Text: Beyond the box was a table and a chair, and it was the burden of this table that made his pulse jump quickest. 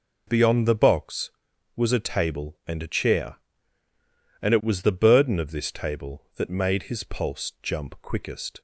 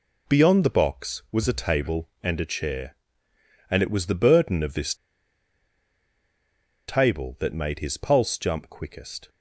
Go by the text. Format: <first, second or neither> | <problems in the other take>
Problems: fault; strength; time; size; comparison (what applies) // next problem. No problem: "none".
first | pauses between "this" and "table"; strong; at 4.9 s; 1.9 s long